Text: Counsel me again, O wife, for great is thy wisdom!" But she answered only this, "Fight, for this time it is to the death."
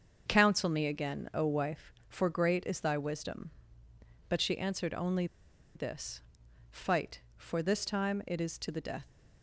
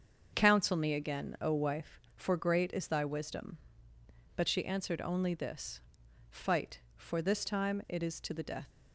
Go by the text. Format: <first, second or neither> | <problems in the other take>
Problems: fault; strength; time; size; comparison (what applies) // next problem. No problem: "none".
second | starts louder than the rest; until 1.2 s; 6.5 dB; also in the second // pauses between "only" and "this"; noticeable; at 5.2 s; 0.50 s long